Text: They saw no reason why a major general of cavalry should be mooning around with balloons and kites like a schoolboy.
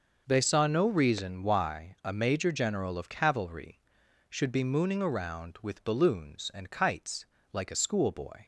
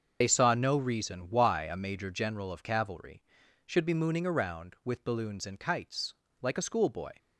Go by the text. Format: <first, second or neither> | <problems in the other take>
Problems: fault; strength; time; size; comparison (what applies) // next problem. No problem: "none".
first | loses the start of "They"; at 0.2 s; 50 ms // starts louder than the rest; until 1.2 s; 6.5 dB // pauses between "kites" and "like"; slight; at 6.1 s; 0.26 s long; slight in the first